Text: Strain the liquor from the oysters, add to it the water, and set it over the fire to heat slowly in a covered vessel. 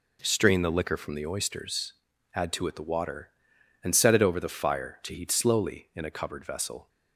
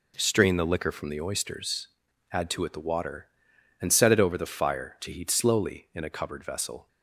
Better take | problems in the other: neither | none

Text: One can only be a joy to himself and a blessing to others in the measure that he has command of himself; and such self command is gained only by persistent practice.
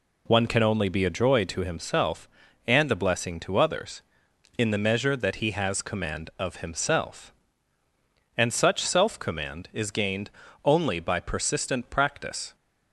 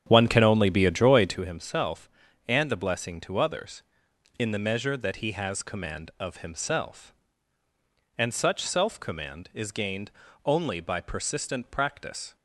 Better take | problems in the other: first | starts louder than the rest; strong; until 1.4 s; 9 dB // pauses between "gained" and "only"; slight; at 10.1 s; 0.34 s long; slight in the first

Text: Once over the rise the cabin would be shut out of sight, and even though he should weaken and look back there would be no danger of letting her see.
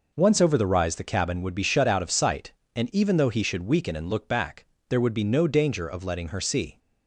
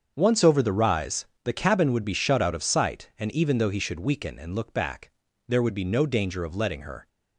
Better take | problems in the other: first | starts louder than the rest; strong; until 1.1 s; 7 dB // pauses between "rise" and "the"; slight; at 1.2 s; 0.22 s long // pauses between "back" and "there"; at 5.0 s; 0.38 s long; slight in the first // stops before "see"; at 7.0 s

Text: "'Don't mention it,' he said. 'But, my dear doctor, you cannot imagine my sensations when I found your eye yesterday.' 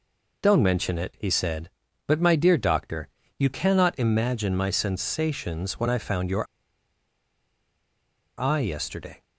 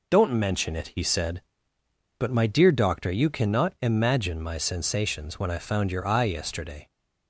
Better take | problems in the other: second | pauses between "your" and "eye"; strong; at 6.4 s; 1.9 s long

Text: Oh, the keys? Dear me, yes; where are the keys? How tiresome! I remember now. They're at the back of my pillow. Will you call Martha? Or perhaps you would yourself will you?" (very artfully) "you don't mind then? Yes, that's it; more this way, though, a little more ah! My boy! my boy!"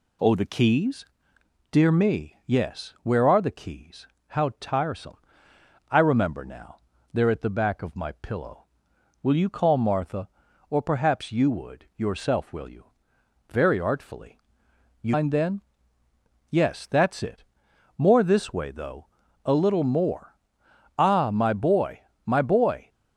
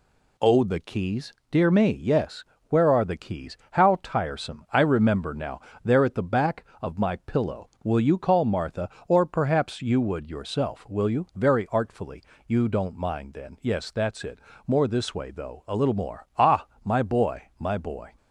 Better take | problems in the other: second | skips "don't"; at 15.1 s // pauses between "more" and "ah"; noticeable; at 20.3 s; 0.62 s long

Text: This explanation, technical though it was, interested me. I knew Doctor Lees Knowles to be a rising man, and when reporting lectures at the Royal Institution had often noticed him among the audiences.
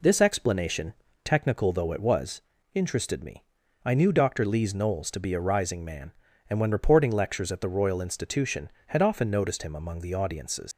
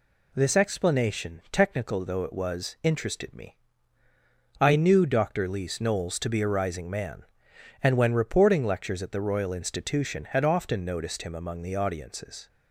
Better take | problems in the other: second | leaves "audiences" unfinished; at 10.7 s; 130 ms

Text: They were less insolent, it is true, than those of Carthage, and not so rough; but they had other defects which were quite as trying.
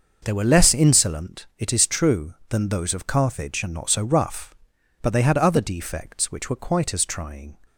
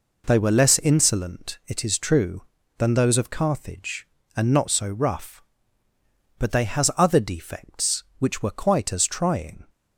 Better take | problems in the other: first | says "has" for "had"; at 6.6 s

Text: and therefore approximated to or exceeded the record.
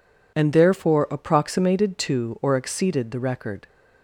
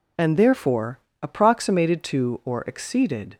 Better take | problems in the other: first | pauses between "therefore" and "approximated"; slight; at 0.9 s; 0.22 s long // stops before "the record"; at 3.3 s

